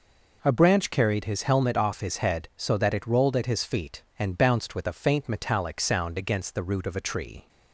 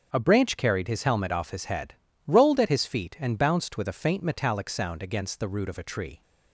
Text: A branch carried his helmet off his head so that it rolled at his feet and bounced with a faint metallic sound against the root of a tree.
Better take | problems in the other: first | starts louder than the rest; strong; until 1.1 s; 7.5 dB // skips "so that it"; at 2.1 s

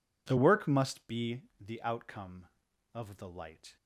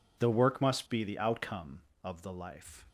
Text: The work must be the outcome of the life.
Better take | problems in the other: second | pauses between "be" and "the"; slight; at 1.4 s; 0.18 s long // says "light" for "life"; at 3.2 s

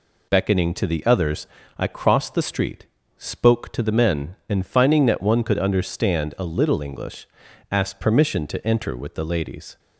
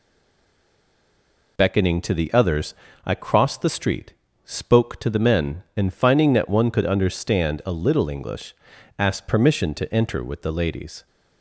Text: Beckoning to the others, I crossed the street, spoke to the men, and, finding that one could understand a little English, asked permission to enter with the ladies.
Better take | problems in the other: first | stays silent before the first word; noticeable; until 1.5 s; 1.5 s long

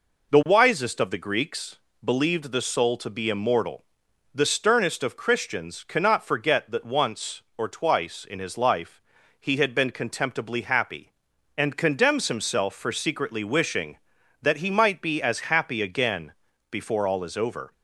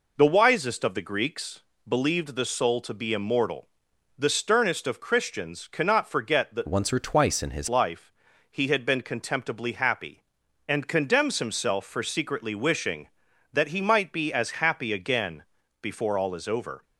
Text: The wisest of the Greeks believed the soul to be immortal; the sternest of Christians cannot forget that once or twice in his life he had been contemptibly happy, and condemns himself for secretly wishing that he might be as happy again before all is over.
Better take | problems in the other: first | pauses between "Greeks" and "believed"; slight; at 1.6 s; 0.28 s long; slight in the first // changes voice from "once" to "his"; from 6.6 to 7.6 s; 1.0 s long // pauses between "life" and "he"; at 8.1 s; 0.38 s long; also in the first // pauses between "again" and "before"; slight; at 15.4 s; 0.36 s long; slight in the first

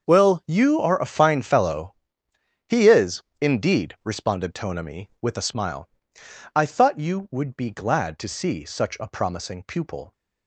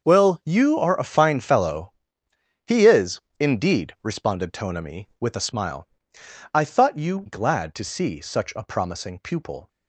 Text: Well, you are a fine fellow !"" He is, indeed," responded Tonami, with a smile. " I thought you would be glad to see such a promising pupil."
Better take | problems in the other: first | starts louder than the rest; until 1.0 s; 6 dB; also in the first // skips "would be"; at 7.2 s

